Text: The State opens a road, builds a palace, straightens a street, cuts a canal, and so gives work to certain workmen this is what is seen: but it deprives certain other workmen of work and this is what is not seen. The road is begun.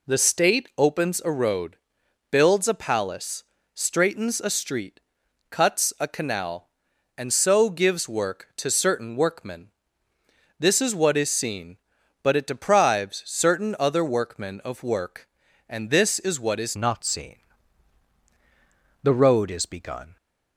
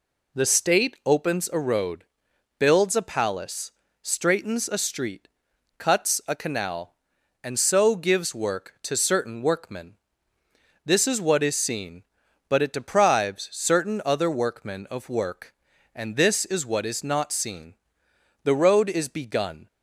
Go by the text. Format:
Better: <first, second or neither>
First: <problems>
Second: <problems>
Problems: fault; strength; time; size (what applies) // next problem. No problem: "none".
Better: second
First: pauses between "workmen" and "this"; noticeable; at 9.6 s; 0.88 s long // changes voice at "not"; from 16.7 s on; 3.4 s long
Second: pauses between "workmen" and "this"; noticeable; at 9.9 s; 0.88 s long